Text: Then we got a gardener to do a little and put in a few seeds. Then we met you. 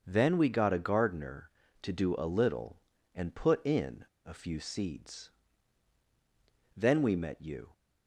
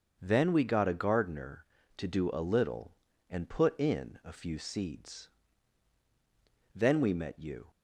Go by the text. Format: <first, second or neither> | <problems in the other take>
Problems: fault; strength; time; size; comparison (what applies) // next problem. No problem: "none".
second | starts louder than the rest; until 1.0 s; 6.5 dB; also in the second // pauses between "in" and "a"; slight; at 4.0 s; 0.19 s long